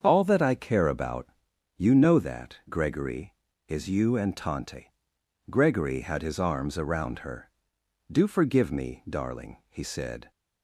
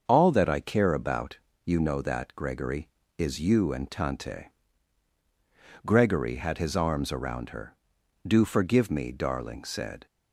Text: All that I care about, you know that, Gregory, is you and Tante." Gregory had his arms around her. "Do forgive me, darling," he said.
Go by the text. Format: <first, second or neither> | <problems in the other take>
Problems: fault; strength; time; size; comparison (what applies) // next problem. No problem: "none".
first | starts louder than the rest; until 1.0 s; 6.5 dB; also in the first // skips "he"; at 9.6 s